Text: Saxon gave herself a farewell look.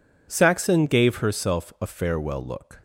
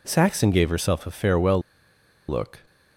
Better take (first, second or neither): first